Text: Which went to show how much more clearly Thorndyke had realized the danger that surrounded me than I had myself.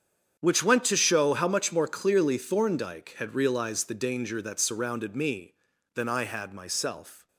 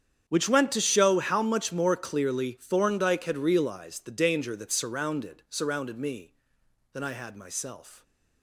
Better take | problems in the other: first | starts louder than the rest; strong; until 1.2 s; 8.5 dB; strong in the first // says "surrounded" twice; at 5.4 s

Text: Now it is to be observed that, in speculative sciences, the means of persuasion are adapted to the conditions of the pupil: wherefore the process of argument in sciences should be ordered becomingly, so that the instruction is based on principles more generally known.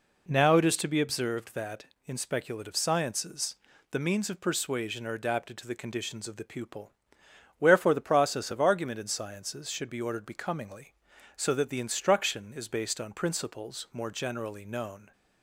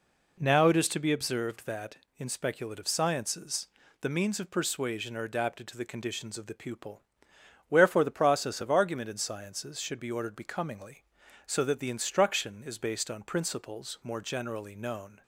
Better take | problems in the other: neither | none

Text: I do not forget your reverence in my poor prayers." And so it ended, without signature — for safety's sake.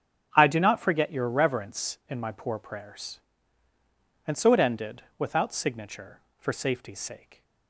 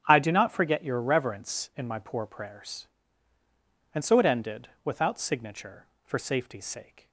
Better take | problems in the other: neither | starts louder than the rest; strong; the same in both

